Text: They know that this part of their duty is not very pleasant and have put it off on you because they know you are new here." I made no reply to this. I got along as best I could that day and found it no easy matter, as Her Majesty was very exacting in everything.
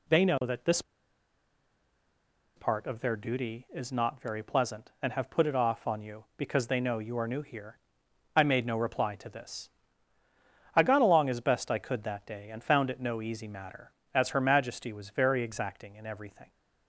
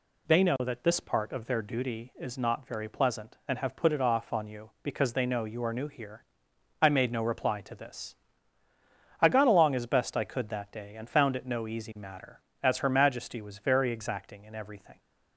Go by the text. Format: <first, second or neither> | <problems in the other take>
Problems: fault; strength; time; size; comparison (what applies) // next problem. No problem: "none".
second | pauses between "this" and "part"; strong; at 0.8 s; 1.7 s long